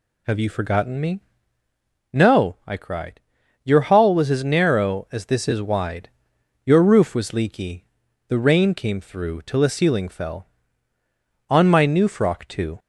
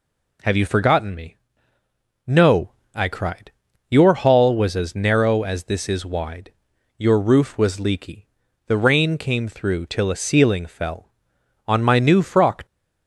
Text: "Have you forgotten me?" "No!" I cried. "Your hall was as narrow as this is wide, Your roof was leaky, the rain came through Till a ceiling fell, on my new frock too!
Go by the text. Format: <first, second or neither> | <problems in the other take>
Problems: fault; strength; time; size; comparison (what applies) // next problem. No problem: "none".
first | stops before "too"; at 12.6 s